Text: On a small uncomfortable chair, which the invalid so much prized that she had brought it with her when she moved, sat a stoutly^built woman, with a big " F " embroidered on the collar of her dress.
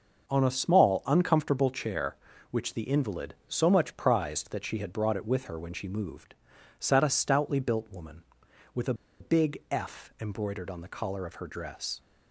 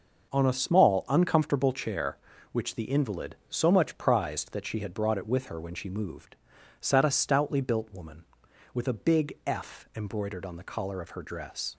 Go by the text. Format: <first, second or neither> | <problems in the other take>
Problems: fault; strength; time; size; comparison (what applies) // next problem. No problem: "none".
second | pauses between "a" and "big"; slight; at 8.9 s; 0.26 s long